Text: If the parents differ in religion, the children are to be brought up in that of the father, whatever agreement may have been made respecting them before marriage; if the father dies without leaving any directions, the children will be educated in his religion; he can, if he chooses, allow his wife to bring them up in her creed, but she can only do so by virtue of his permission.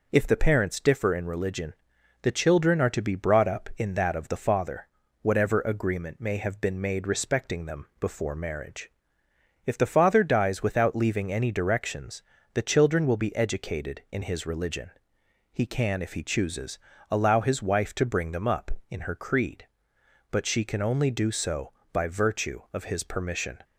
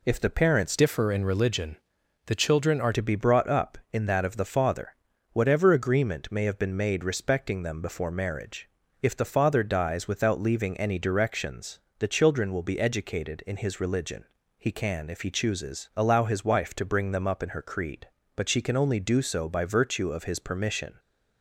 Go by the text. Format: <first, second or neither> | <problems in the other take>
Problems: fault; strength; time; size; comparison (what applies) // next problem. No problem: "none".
first | changes voice from "differ" to "are"; from 0.7 to 2.9 s; 2.2 s long